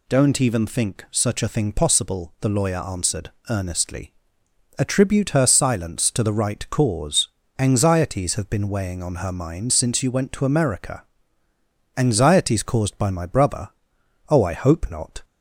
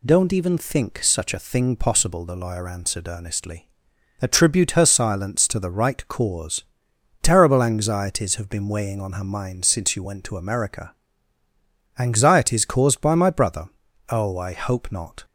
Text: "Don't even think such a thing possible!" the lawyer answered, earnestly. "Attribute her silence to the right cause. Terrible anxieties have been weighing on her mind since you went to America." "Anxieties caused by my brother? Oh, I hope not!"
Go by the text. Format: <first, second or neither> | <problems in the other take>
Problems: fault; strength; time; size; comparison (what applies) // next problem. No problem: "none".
second | skips "Terrible"; at 7.4 s